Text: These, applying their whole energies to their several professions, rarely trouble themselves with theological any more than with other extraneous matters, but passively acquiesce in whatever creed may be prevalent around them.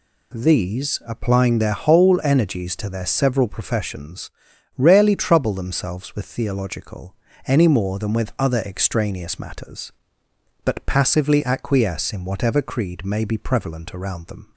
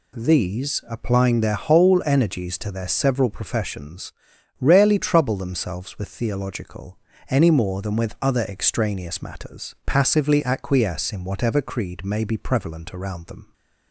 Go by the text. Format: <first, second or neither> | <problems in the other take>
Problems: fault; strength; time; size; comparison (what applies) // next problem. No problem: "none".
first | pauses between "theological" and "any"; slight; at 6.9 s; 0.32 s long; slight in the first // skips "but"; at 9.7 s